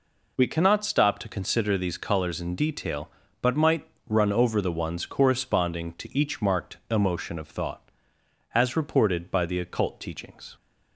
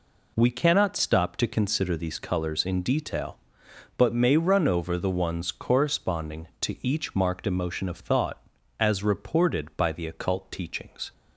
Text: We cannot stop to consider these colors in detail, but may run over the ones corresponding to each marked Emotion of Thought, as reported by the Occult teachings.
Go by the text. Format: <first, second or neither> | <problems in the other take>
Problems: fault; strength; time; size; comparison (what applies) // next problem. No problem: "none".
second | says "might" for "may"; at 3.5 s